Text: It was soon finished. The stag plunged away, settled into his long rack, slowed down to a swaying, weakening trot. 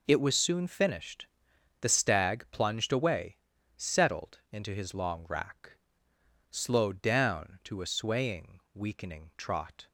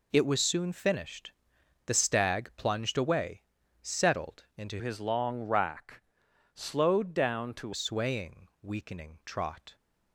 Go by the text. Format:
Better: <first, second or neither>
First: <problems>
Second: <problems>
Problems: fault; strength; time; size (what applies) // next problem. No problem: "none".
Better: first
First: none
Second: changes voice from "his" to "to"; from 4.7 to 7.7 s; 3.0 s long